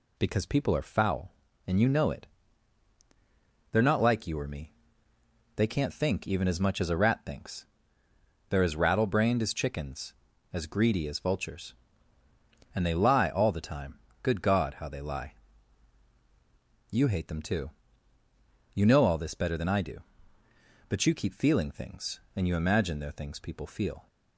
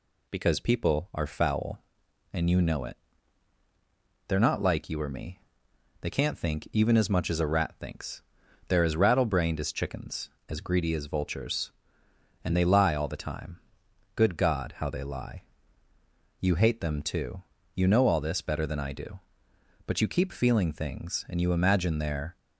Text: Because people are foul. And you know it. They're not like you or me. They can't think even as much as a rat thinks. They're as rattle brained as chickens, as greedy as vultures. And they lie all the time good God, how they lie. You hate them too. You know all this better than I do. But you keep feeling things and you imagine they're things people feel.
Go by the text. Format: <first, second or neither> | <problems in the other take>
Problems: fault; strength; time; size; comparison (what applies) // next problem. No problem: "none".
first | pauses between "time" and "good"; noticeable; at 13.5 s; 0.58 s long; slight in the first // stops before "things people feel"; at 22.3 s